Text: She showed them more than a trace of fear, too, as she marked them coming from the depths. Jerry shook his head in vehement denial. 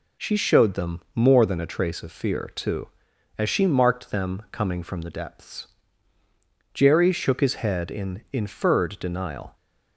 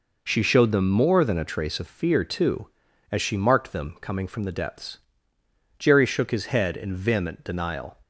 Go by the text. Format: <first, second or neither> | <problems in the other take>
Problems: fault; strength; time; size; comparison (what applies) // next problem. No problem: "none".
second | says "inferred" for "vehement"; at 8.3 s